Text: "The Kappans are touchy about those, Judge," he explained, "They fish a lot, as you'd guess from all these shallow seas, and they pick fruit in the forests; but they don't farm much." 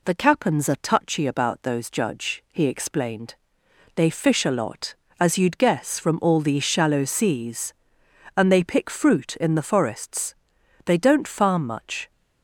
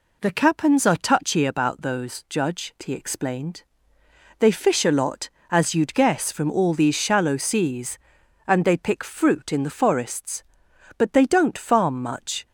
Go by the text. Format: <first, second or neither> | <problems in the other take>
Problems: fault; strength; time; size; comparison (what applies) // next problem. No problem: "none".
second | skips "but"; at 10.5 s